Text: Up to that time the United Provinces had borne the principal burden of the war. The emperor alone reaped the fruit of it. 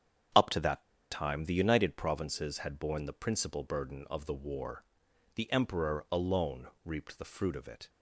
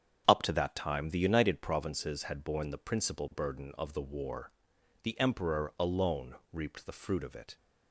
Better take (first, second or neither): second